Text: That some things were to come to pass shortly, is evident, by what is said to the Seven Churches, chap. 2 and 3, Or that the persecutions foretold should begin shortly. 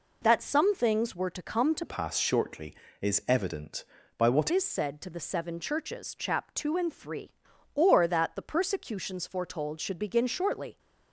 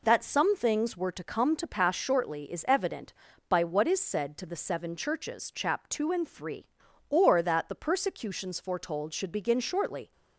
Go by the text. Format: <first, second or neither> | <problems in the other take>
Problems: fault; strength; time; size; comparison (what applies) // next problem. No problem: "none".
second | changes voice from "pass" to "what"; from 1.8 to 4.5 s; 2.7 s long